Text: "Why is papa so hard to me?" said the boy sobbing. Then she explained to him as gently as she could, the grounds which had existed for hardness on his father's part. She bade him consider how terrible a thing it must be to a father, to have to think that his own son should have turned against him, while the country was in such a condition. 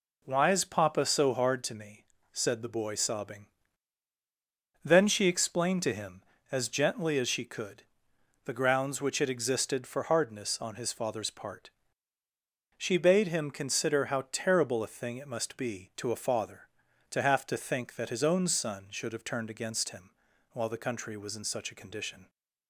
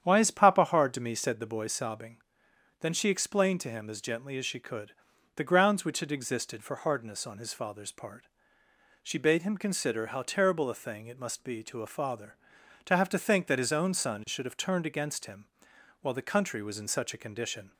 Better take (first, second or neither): first